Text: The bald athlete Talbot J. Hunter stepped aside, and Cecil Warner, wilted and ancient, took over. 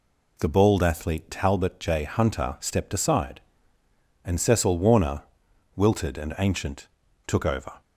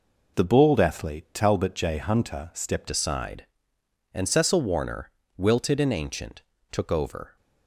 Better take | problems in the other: first | changes voice at "aside"; from 2.8 s on; 4.5 s long

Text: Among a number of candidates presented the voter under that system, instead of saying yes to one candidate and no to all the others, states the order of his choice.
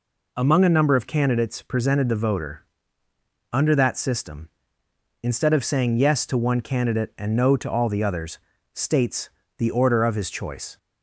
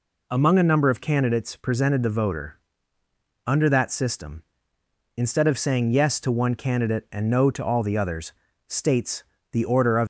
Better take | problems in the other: first | pauses between "voter" and "under"; noticeable; at 2.5 s; 0.86 s long; noticeable in the first // pauses between "states" and "the"; slight; at 9.2 s; 0.30 s long; slight in the first // stops before "his choice"; at 10.0 s

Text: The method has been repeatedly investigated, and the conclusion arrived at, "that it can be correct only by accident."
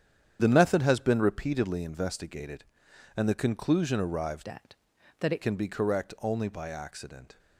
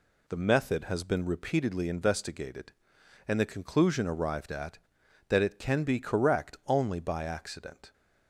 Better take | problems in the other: second | starts louder than the rest; strong; until 1.4 s; 9 dB // changes voice from "at" to "it"; from 4.4 to 5.4 s; 1.0 s long

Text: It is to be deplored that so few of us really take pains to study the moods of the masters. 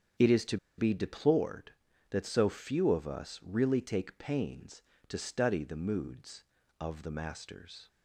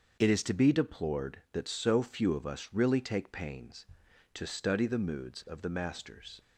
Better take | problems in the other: second | starts louder than the rest; strong; until 1.4 s; 8 dB; also in the second // pauses between "to" and "be"; slight; at 0.5 s; 0.21 s long

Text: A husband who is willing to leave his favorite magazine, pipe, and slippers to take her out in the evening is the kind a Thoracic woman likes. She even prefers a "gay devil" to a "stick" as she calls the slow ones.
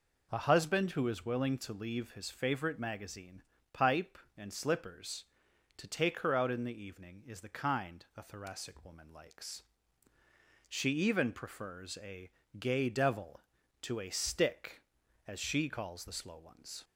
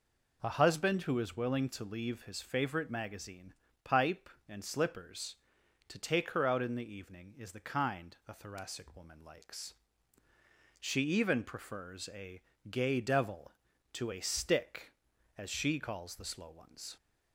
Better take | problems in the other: neither | pauses between "a" and "gay"; slight; the same in both

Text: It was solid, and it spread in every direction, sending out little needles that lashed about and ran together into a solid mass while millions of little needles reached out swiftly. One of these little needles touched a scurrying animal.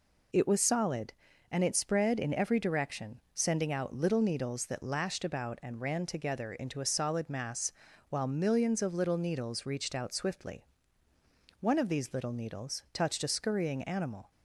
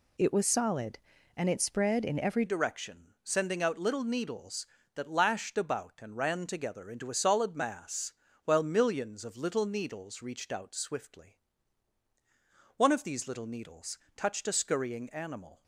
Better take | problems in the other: first | changes voice at "direction"; from 2.4 s on; 13.2 s long // pauses between "mass" and "while"; slight; at 8.1 s; 0.32 s long; also in the first // pauses between "needles" and "touched"; slight; at 13.9 s; 0.18 s long

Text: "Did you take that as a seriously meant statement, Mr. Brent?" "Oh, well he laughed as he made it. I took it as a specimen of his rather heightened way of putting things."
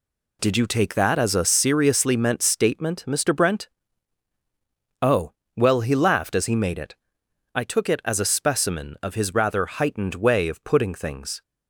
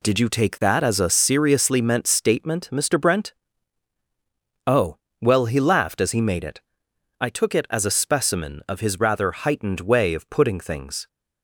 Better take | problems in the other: neither | none

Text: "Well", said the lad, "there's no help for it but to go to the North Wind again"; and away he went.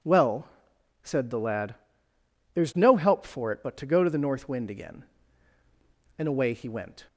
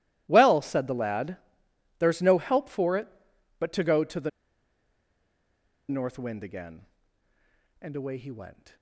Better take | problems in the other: first | pauses between "the" and "North"; strong; at 4.2 s; 1.5 s long

